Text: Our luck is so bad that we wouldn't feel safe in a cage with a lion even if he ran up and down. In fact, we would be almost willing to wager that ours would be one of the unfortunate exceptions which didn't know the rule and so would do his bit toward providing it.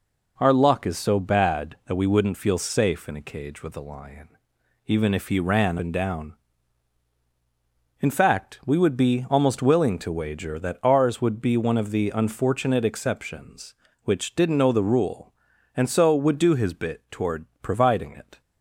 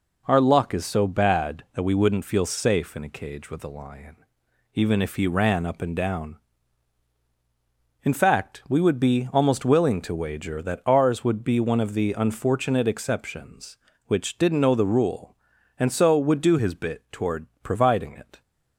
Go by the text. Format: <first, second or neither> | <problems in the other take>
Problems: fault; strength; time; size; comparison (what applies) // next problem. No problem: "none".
second | pauses between "lion" and "even"; noticeable; at 4.2 s; 0.58 s long; noticeable in the second // skips "up"; at 5.7 s // pauses between "toward" and "providing"; slight; at 17.4 s; 0.16 s long; slight in the second